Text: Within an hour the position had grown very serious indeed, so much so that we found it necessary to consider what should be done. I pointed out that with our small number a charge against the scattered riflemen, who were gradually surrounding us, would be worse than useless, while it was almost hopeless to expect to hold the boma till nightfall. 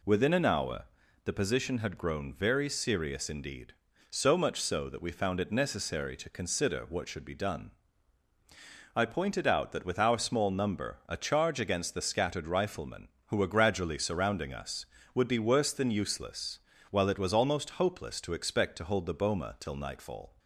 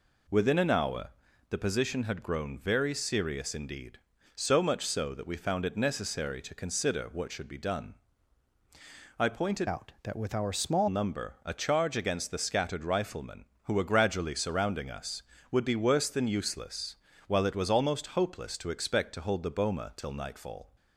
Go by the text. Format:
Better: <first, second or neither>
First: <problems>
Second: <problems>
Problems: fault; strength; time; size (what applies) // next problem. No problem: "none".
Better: first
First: pauses between "hour" and "the"; at 0.8 s; 0.40 s long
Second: pauses between "hour" and "the"; at 1.1 s; 0.40 s long // changes voice from "out" to "small"; from 9.6 to 10.8 s; 1.2 s long